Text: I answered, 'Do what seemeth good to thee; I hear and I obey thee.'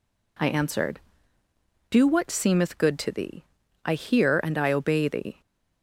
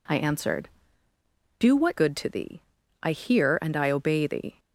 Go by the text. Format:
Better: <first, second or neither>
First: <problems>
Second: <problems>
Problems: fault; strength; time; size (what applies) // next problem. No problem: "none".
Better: first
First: none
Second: skips "seemeth"; at 1.9 s